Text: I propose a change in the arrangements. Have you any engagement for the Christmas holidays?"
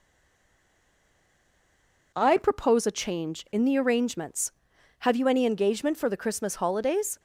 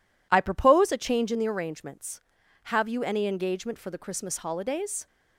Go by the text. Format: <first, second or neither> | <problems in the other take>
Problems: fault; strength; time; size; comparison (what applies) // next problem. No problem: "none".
second | stays silent before the first word; until 2.1 s; 2.1 s long